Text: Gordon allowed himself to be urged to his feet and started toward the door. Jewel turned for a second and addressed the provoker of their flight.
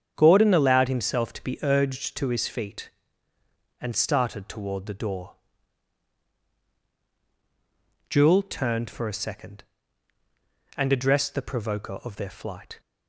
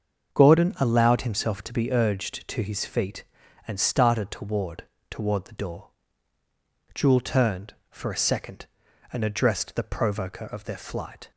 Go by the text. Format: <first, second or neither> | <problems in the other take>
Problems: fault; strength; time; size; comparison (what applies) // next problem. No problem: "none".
first | starts louder than the rest; until 1.3 s; 6.5 dB; strong in the first // says "toward" twice; at 5.0 s